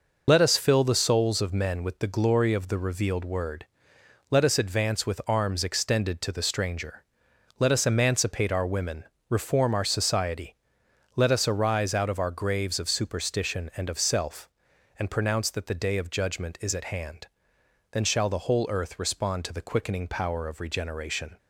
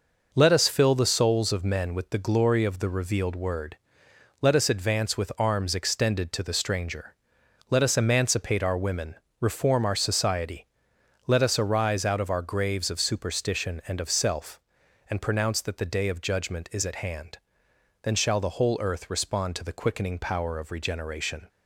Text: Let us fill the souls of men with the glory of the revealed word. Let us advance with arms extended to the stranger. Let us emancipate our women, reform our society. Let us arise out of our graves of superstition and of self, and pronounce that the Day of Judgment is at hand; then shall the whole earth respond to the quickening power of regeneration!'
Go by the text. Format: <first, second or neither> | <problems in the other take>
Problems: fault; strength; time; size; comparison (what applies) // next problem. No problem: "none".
second | loses the start of "Let"; at 0.2 s; 50 ms